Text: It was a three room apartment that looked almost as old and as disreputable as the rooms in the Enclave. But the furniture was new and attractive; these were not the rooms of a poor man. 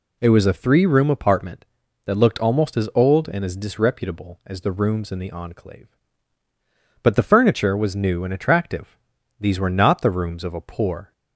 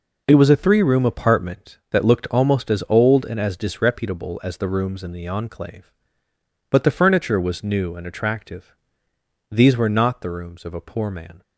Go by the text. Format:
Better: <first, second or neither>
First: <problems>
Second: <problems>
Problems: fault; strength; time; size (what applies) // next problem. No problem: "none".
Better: second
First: stops before "man"; at 11.1 s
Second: none